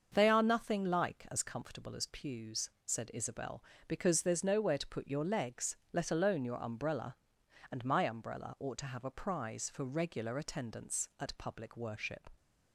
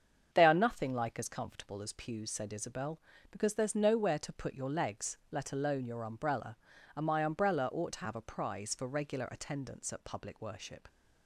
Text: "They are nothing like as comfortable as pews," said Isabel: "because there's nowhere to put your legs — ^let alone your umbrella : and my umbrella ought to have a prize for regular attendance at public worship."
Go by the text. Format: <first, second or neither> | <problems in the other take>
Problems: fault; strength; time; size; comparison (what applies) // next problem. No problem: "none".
neither | starts louder than the rest; the same in both